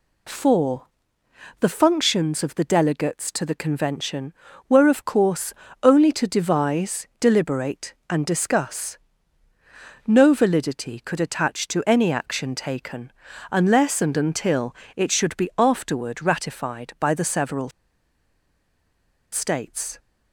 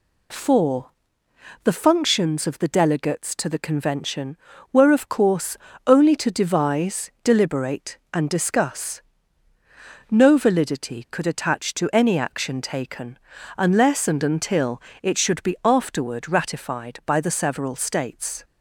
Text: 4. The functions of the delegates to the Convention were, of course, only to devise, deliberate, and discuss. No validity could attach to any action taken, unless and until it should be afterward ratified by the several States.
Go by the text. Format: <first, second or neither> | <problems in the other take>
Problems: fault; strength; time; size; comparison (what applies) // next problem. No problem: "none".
second | pauses between "until" and "it"; slight; at 14.7 s; 0.20 s long; slight in the second // pauses between "several" and "States"; strong; at 17.6 s; 1.6 s long